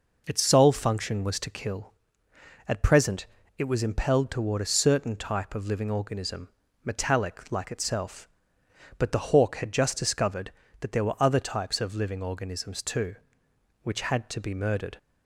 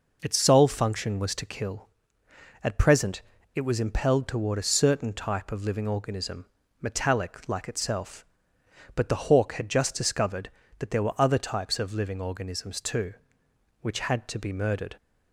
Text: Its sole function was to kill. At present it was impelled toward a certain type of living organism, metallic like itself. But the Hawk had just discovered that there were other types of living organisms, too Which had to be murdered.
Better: neither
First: pauses between "present" and "it"; slight; at 3.2 s; 0.30 s long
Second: pauses between "present" and "it"; slight; at 3.2 s; 0.31 s long

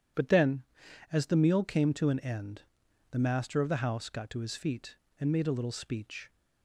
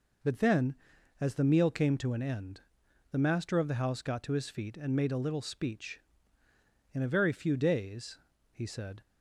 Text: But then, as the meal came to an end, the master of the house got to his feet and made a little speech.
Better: first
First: none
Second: goes on to say "In a very few days he said"; strong; from 6.9 s on; 2.0 s long

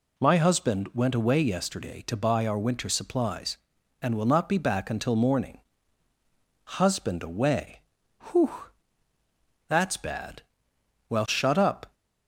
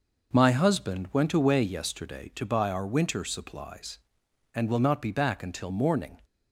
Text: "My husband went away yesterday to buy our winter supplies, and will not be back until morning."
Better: second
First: goes on to say "Husband away Whew that's bad Well shut up"; strong; from 6.6 s on; 5.2 s long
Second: none

